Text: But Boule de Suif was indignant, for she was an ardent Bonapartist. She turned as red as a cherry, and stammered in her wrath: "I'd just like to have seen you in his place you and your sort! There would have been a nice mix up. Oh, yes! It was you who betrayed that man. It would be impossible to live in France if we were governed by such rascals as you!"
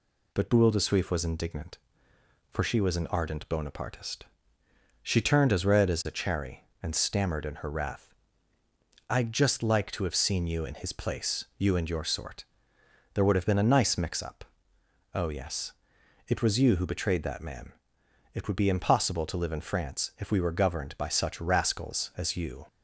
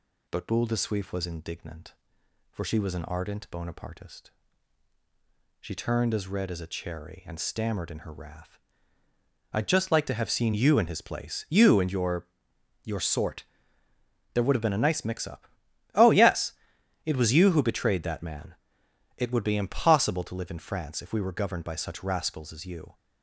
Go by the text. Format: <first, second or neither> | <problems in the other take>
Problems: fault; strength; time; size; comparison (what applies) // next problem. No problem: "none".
first | says "your" twice; at 12.8 s